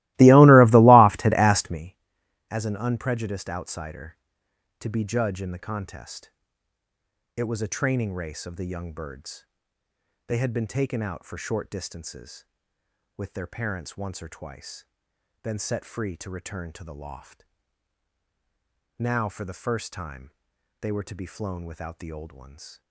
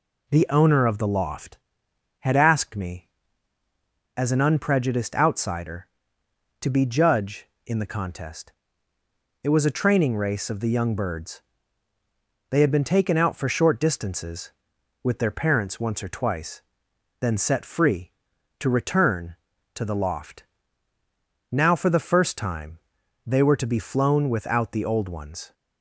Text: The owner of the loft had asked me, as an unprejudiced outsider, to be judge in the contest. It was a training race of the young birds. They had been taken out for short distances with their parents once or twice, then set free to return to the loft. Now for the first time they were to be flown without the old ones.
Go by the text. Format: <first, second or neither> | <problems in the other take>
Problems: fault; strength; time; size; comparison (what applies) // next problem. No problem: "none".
second | starts louder than the rest; strong; until 1.9 s; 19.5 dB // pauses between "time" and "they"; noticeable; at 20.3 s; 0.48 s long; noticeable in the second